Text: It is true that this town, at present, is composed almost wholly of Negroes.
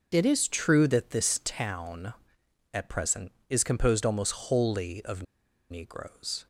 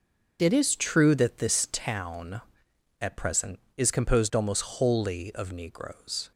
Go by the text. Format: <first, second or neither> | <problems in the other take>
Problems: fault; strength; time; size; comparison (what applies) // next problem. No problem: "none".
second | starts louder than the rest; noticeable; until 1.1 s; 6 dB; also in the second // pauses between "of" and "Negroes"; noticeable; at 5.2 s; 0.47 s long